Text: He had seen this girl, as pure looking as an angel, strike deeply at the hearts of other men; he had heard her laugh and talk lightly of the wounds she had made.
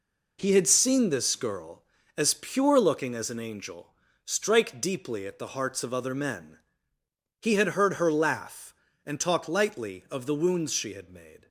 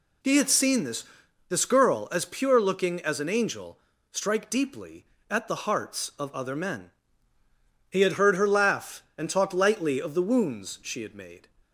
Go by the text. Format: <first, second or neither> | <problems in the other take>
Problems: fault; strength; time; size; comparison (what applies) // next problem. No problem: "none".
first | says "this" twice; at 1.4 s